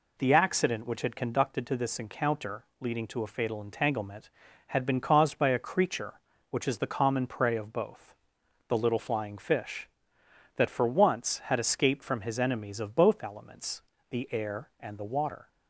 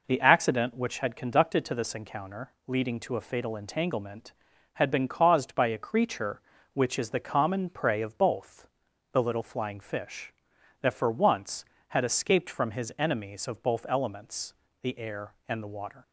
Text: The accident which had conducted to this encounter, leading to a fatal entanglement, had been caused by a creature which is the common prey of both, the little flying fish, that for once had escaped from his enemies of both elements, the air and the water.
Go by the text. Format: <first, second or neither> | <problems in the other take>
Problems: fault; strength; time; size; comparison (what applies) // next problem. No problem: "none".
neither | none